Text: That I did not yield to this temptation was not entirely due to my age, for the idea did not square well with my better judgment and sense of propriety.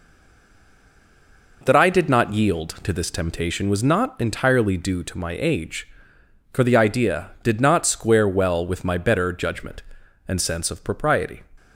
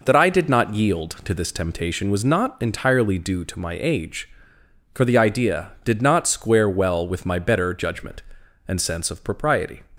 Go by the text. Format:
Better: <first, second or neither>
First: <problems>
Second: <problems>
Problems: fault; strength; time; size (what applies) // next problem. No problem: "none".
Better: second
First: stays silent before the first word; noticeable; until 1.6 s; 1.6 s long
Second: none